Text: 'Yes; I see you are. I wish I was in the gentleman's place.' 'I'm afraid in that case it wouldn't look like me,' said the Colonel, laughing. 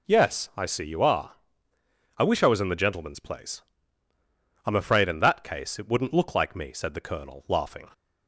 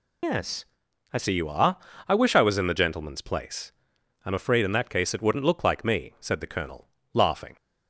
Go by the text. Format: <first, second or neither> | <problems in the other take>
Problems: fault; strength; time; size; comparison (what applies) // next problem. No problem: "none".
first | loses the start of "Yes"; at 0.2 s; 85 ms